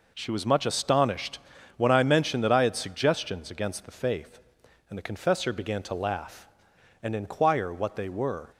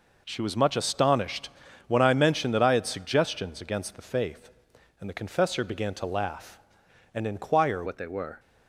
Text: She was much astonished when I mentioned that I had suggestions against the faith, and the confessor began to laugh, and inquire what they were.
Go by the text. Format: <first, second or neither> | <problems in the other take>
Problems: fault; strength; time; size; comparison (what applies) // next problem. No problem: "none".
first | pauses between "astonished" and "when"; at 1.4 s; 0.38 s long; also in the first // changes voice at "what"; from 7.8 s on; 0.5 s long